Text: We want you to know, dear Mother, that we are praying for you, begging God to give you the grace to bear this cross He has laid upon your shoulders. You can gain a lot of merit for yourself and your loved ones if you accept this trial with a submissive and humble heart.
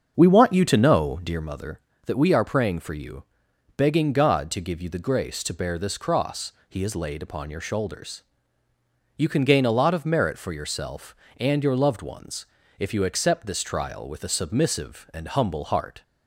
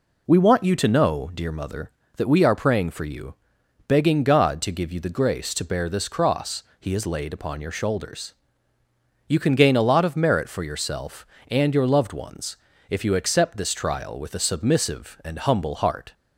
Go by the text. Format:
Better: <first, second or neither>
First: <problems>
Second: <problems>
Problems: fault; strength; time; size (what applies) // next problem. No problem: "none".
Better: second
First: starts louder than the rest; until 1.5 s; 7 dB // pauses between "cross" and "He"; slight; at 6.5 s; 0.16 s long // pauses between "ones" and "if"; slight; at 12.4 s; 0.32 s long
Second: pauses between "cross" and "He"; slight; at 6.6 s; 0.16 s long // pauses between "ones" and "if"; slight; at 12.5 s; 0.32 s long